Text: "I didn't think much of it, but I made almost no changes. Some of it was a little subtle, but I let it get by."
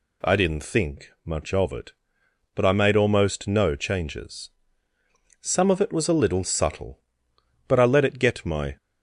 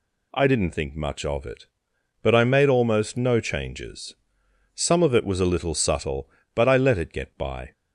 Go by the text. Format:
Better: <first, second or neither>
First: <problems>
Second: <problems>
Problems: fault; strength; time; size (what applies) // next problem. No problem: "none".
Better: second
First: says "my" for "by"; at 8.4 s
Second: none